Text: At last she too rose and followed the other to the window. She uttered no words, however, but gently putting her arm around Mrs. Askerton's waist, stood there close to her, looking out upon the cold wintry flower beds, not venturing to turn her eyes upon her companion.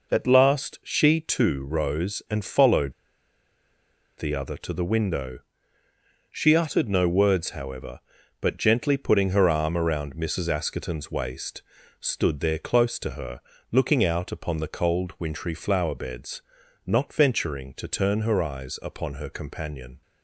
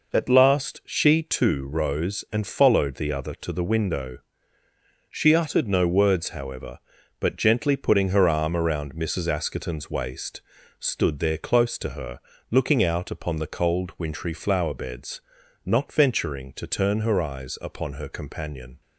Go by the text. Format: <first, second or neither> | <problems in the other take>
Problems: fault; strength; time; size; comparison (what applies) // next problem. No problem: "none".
second | pauses between "followed" and "the"; strong; at 2.9 s; 1.2 s long